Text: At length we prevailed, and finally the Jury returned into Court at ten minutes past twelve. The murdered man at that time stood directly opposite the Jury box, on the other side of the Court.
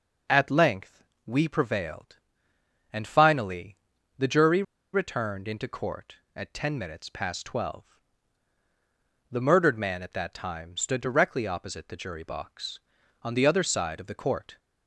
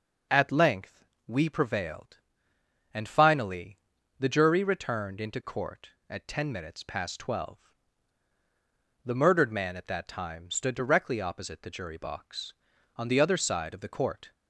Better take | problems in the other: second | pauses between "length" and "we"; slight; at 1.0 s; 0.22 s long; slight in the second // pauses between "finally" and "the"; at 3.7 s; 0.40 s long; also in the second // pauses between "Jury" and "returned"; slight; at 4.6 s; 0.31 s long

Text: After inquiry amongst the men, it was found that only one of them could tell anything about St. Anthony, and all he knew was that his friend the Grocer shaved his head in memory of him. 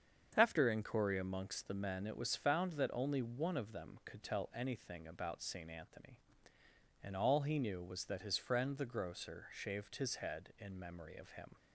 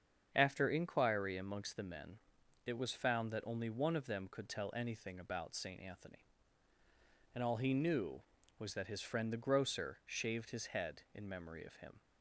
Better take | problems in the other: neither | starts louder than the rest; strong; the same in both

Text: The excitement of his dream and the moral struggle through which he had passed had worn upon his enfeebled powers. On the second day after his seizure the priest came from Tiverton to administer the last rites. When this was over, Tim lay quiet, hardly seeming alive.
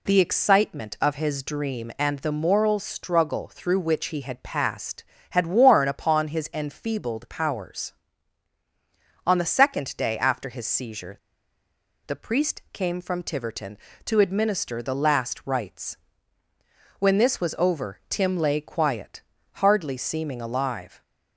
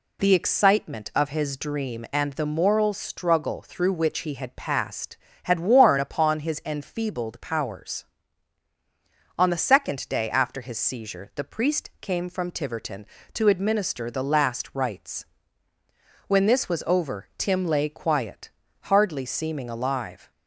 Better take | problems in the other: second | pauses between "seizure" and "the"; noticeable; at 11.1 s; 0.89 s long

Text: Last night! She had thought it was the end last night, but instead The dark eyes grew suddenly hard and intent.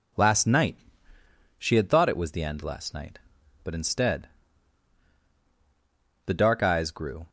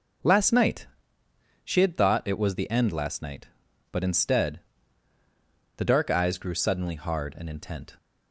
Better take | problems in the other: second | pauses between "instead" and "The"; strong; at 4.2 s; 1.9 s long; also in the second // stops before "suddenly hard and intent"; at 7.2 s

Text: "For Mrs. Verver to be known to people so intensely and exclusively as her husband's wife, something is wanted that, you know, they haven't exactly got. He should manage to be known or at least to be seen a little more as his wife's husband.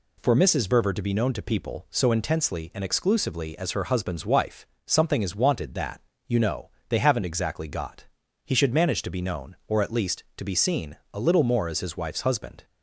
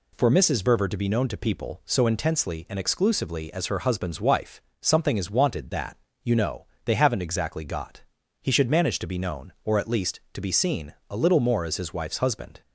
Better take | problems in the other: neither | pauses between "seen" and "a"; slight; the same in both

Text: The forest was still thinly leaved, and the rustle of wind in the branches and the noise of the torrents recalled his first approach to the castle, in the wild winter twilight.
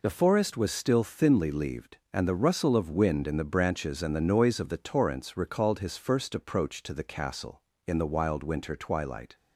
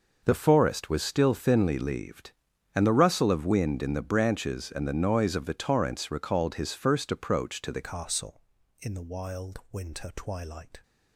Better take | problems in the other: first | changes voice at "castle"; from 7.8 s on; 3.0 s long

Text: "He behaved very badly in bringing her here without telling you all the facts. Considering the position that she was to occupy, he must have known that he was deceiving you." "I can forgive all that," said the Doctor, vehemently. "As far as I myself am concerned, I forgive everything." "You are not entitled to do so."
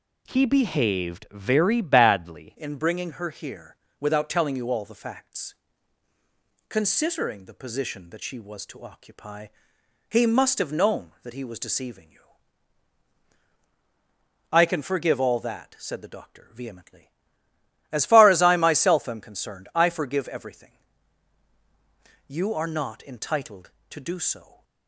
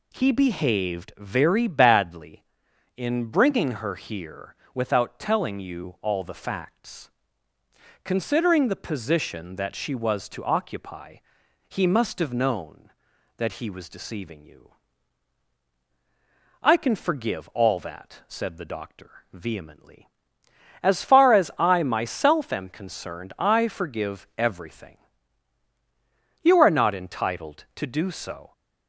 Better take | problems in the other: second | changes voice at "in"; from 2.5 s on; 22.1 s long // pauses between "here" and "without"; slight; at 3.7 s; 0.24 s long; slight in the second

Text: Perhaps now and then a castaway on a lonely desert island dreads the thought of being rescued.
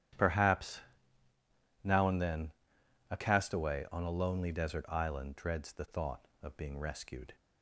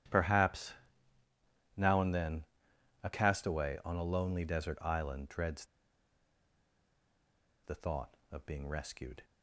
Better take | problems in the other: first | starts louder than the rest; strong; until 2.1 s; 11 dB; strong in the first // pauses between "Perhaps" and "now"; at 0.7 s; 1.0 s long; also in the first // pauses between "then" and "a"; noticeable; at 2.4 s; 0.58 s long; noticeable in the first // pauses between "dreads" and "the"; strong; at 5.6 s; 1.9 s long

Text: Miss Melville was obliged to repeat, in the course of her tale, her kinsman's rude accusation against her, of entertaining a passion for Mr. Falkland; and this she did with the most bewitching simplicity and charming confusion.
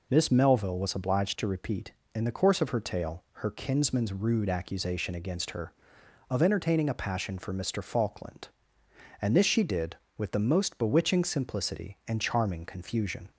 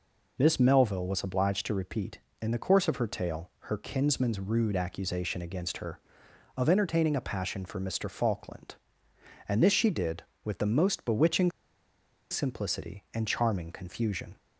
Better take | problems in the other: first | pauses between "bewitching" and "simplicity"; noticeable; at 11.5 s; 0.79 s long

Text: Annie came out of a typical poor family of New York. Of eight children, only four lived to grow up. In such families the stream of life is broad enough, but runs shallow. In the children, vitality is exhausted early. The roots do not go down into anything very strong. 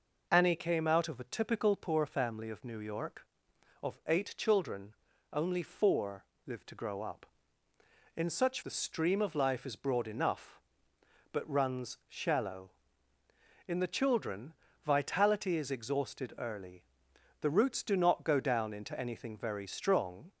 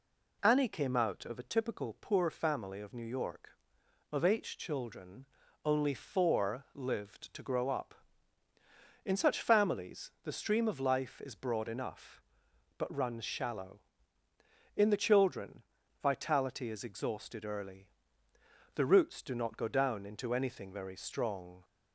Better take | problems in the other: second | pauses between "four" and "lived"; slight; at 6.2 s; 0.22 s long // skips "families"; at 8.6 s

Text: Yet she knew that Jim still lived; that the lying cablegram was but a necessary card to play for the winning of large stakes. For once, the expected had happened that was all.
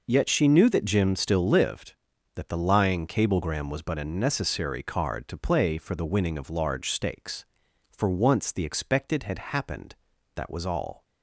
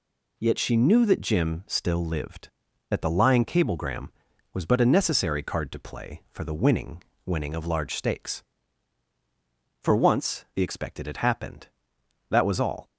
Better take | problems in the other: first | says "winning" twice; at 7.2 s

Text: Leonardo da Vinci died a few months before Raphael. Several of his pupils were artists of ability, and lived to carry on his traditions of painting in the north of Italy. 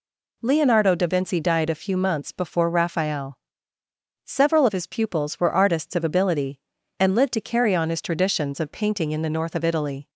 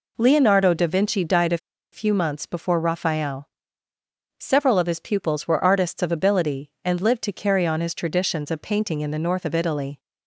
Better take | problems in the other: first | pauses between "a" and "few"; slight; at 1.5 s; 0.35 s long

